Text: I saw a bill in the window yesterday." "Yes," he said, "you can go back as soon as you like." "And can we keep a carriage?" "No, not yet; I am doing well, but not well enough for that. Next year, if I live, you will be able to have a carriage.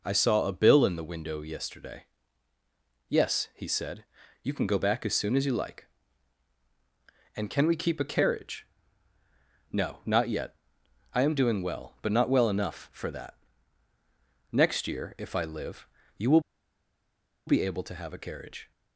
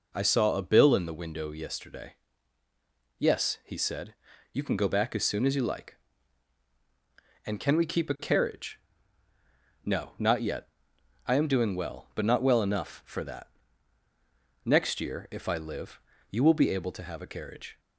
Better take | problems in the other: second | pauses between "will" and "be"; at 16.4 s; 1.0 s long

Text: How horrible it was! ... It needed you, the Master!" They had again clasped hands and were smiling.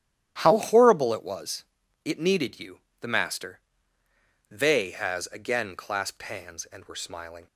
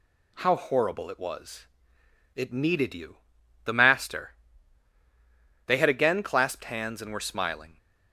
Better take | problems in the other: second | starts louder than the rest; strong; until 1.4 s; 11.5 dB // says "has" for "had"; at 4.9 s

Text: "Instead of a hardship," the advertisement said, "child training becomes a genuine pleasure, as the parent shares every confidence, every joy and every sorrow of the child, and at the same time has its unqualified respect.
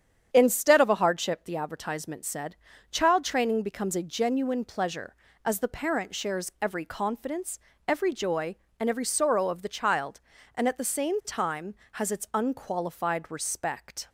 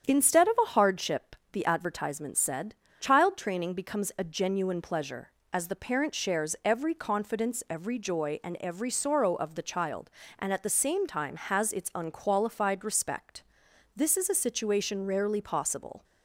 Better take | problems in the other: first | starts louder than the rest; strong; until 1.1 s; 8.5 dB; strong in the first // goes on to say "This is a situation rarely possible"; strong; from 13.9 s on; 2.0 s long

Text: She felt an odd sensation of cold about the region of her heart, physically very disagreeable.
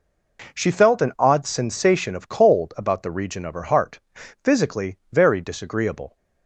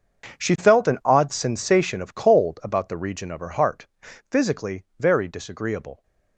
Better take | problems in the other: first | gets quieter; strong; throughout; 15.5 dB // pauses between "physically" and "very"; slight; at 4.8 s; 0.16 s long; slight in the first

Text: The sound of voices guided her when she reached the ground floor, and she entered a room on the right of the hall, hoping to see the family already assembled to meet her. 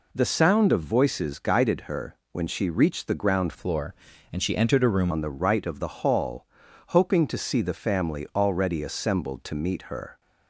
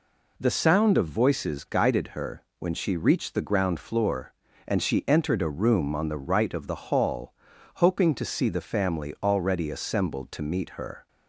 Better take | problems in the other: second | pauses between "her" and "when"; slight; at 2.1 s; 0.16 s long; slight in the second // changes voice from "floor" to "room"; from 3.5 to 5.1 s; 1.6 s long

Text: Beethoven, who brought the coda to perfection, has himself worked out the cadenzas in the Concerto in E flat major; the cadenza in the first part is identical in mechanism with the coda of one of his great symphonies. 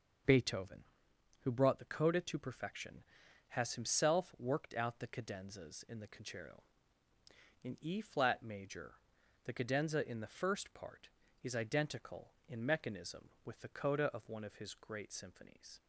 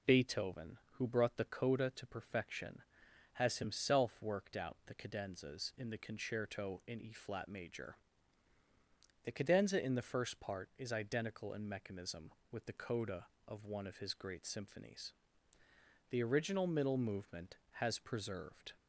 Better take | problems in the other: first | goes on to say "The original middle movement has preserved"; strong; from 16.0 s on; 2.6 s long

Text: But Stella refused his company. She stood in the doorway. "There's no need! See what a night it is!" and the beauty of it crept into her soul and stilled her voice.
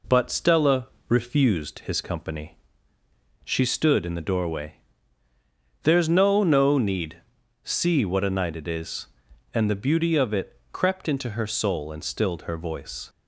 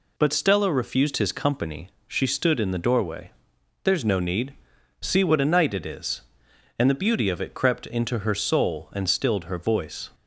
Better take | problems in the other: second | pauses between "Stella" and "refused"; slight; at 0.8 s; 0.22 s long // says "no" twice; at 6.4 s

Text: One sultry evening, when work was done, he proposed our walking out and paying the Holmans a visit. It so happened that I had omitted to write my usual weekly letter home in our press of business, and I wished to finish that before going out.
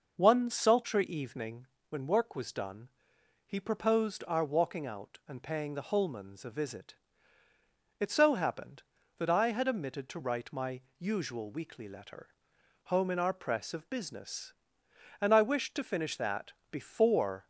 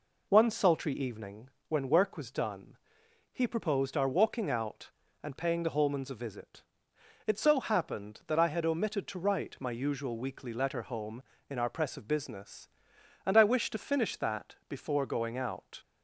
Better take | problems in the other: second | pauses between "my" and "usual"; slight; at 10.7 s; 0.18 s long // pauses between "letter" and "home"; noticeable; at 12.2 s; 0.56 s long // pauses between "that" and "before"; slight; at 16.5 s; 0.20 s long // stops before "going out"; at 17.4 s

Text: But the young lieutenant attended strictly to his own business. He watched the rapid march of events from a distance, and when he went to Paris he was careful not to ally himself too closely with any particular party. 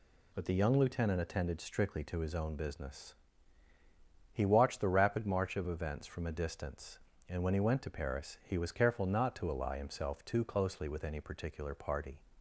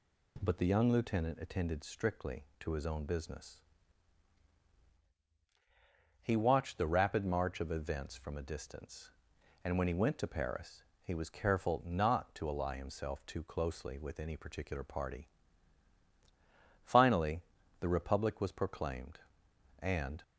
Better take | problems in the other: first | pauses between "Paris" and "he"; slight; at 10.8 s; 0.20 s long // goes on to say "Finally the Republic was proclaimed and"; strong; from 16.8 s on; 3.3 s long

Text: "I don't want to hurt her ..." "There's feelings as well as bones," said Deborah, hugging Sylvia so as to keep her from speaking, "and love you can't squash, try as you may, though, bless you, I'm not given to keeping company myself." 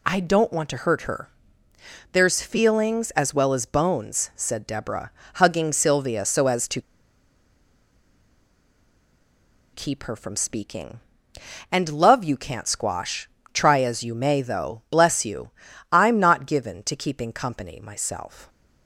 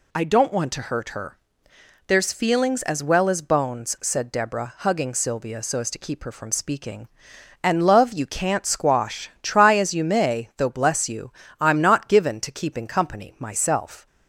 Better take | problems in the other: second | pauses between "to" and "keep"; strong; at 6.8 s; 2.9 s long

